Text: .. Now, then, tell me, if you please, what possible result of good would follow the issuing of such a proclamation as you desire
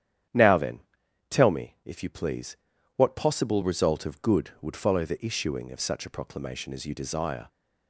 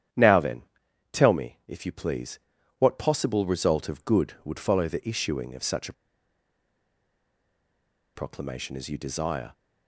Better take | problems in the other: first | starts louder than the rest; strong; until 1.7 s; 10 dB; strong in the first // pauses between "a" and "proclamation"; strong; at 5.9 s; 2.2 s long

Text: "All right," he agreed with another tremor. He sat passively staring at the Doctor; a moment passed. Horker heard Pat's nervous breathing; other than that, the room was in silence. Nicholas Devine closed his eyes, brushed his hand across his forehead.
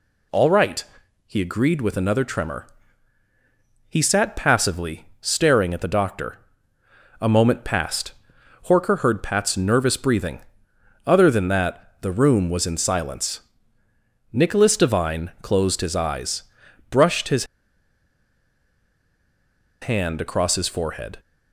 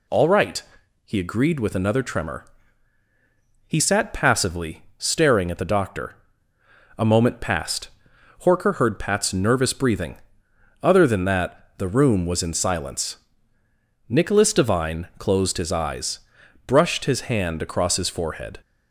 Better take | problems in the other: second | pauses between "passively" and "staring"; slight; at 5.0 s; 0.16 s long; slight in the second // pauses between "his" and "hand"; strong; at 17.4 s; 2.3 s long

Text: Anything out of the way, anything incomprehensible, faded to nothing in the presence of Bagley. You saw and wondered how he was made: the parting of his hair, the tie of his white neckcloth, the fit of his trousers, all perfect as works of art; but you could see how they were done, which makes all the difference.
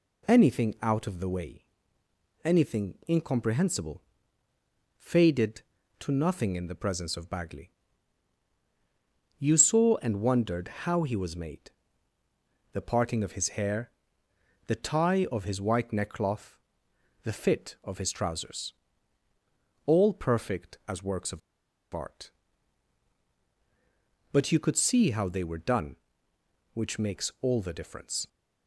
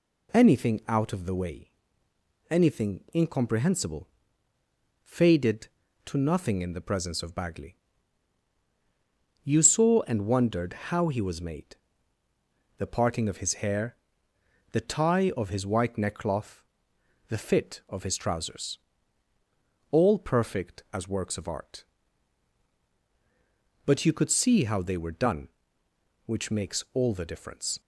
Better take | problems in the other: second | pauses between "wondered" and "how"; slight; at 10.6 s; 0.16 s long; slight in the second // pauses between "of" and "art"; noticeable; at 21.3 s; 0.53 s long

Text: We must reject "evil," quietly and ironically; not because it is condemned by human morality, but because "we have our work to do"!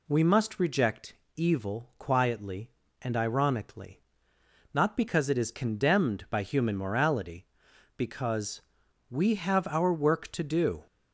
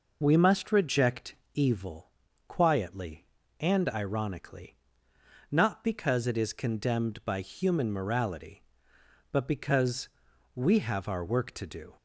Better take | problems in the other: second | pauses between "reject" and "evil"; slight; at 1.1 s; 0.22 s long; slight in the second // skips "but"; at 7.7 s // pauses between "because" and "we"; noticeable; at 8.5 s; 0.50 s long; also in the second

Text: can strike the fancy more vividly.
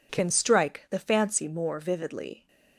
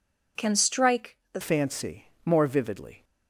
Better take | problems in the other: first | pauses between "strike" and "the"; slight; at 1.1 s; 0.16 s long // changes voice at "fancy"; from 1.4 s on; 1.6 s long // pauses between "fancy" and "more"; slight; at 2.0 s; 0.18 s long

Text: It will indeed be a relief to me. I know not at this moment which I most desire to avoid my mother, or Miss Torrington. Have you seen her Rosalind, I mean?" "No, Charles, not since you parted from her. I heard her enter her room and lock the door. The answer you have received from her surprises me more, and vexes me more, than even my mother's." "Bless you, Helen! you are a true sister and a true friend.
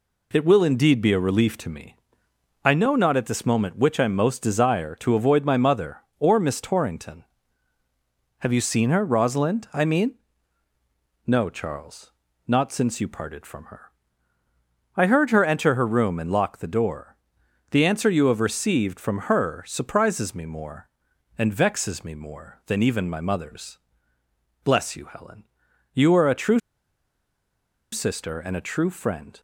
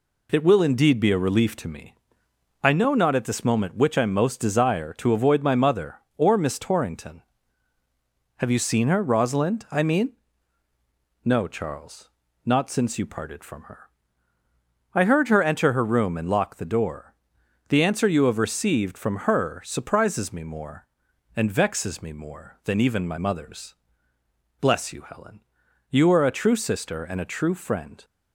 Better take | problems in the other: second | pauses between "true" and "sister"; strong; at 26.5 s; 1.3 s long

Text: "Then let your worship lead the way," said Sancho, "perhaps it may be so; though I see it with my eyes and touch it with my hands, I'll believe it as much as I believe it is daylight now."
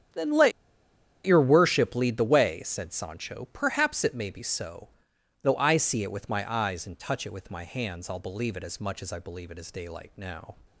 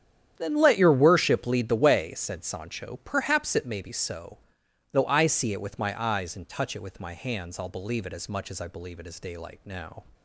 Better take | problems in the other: second | starts louder than the rest; strong; until 1.8 s; 9.5 dB; strong in the second // pauses between "let" and "your"; noticeable; at 0.5 s; 0.73 s long

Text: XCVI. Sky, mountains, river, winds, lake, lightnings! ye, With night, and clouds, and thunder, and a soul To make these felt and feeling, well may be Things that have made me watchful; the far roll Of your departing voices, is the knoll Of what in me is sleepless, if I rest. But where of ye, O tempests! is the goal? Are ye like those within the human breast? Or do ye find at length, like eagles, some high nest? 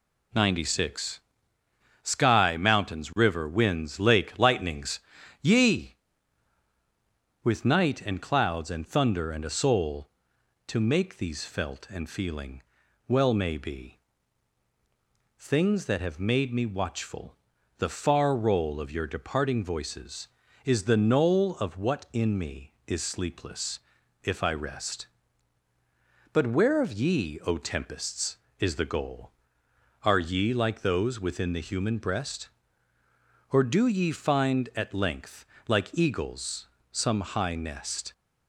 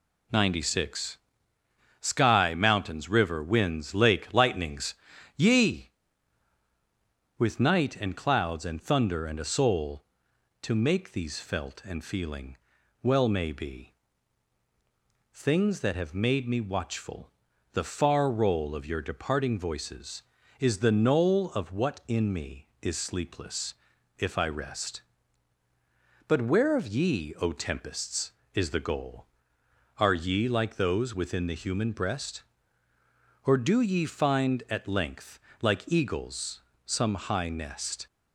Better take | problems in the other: neither | pauses between "be" and "Things"; strong; the same in both

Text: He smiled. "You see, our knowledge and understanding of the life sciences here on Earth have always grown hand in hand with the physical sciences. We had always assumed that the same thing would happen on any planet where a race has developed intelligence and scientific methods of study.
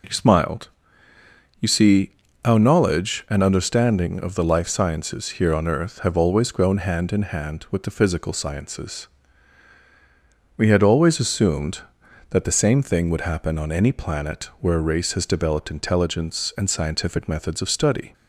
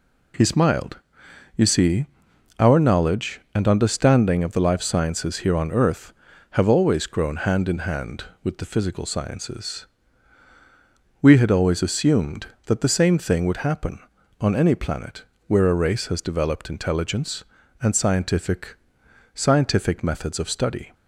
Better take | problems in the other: first | pauses between "planet" and "where"; slight; at 15.2 s; 0.24 s long // says "scientific" twice; at 19.3 s

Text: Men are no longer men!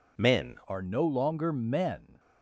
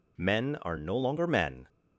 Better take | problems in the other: second | changes voice at "are"; from 0.6 s on; 1.5 s long

